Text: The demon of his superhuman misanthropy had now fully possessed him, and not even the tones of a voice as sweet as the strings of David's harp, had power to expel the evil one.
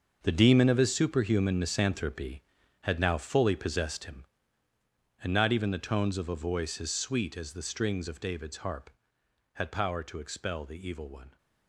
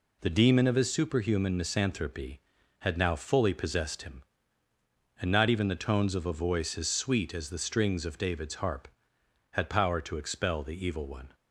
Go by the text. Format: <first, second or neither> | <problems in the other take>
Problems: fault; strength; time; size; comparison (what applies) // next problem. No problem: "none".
second | gets quieter; strong; throughout; 12.5 dB